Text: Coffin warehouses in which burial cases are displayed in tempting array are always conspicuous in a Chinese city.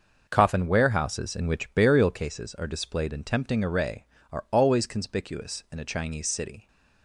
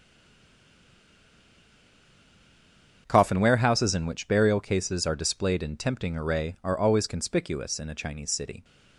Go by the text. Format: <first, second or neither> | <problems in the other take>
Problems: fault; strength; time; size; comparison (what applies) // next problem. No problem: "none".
first | stays silent before the first word; strong; until 3.0 s; 3.0 s long // starts louder than the rest; strong; until 4.0 s; 7.5 dB